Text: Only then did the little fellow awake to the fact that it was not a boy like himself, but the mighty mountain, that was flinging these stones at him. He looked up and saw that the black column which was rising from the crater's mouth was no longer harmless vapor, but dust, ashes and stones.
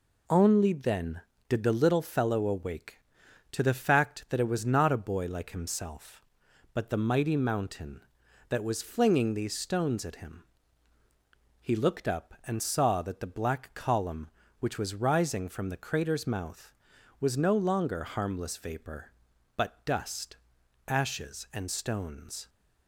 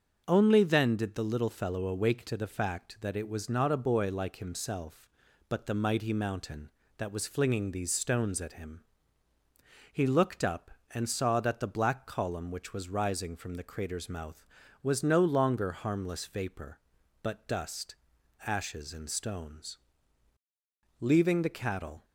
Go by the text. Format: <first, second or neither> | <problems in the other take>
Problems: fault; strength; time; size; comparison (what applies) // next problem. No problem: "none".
first | starts louder than the rest; until 1.2 s; 7 dB // goes on to say "Leaving the cattle"; noticeable; from 21.0 s on; 1.0 s long